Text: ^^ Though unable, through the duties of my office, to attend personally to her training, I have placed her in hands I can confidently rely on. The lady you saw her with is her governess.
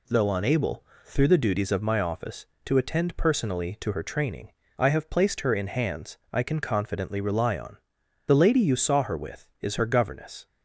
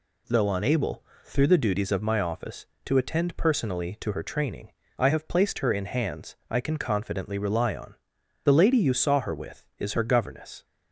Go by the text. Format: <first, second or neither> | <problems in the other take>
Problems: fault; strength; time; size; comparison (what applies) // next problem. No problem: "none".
neither | none